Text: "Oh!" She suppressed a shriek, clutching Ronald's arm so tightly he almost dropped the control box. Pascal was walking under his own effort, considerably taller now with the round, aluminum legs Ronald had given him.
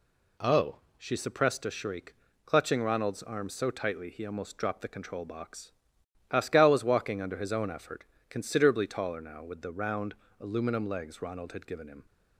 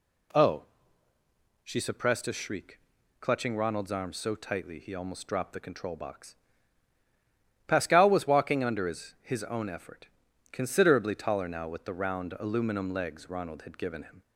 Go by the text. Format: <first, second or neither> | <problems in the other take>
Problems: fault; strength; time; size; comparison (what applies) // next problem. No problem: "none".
first | says "his" twice; at 9.2 s